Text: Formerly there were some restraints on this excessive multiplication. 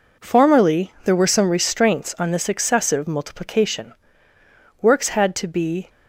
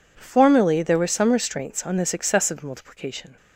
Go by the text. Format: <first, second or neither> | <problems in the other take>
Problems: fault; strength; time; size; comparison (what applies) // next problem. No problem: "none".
second | goes on to say "Works had to be"; noticeable; from 4.8 s on; 1.0 s long